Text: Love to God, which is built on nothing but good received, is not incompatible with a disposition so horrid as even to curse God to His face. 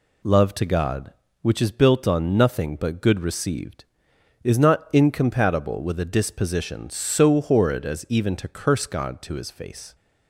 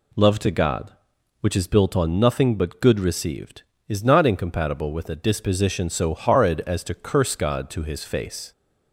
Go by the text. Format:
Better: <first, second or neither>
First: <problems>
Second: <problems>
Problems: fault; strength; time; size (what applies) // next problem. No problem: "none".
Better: first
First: none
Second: skips "even"; at 6.8 s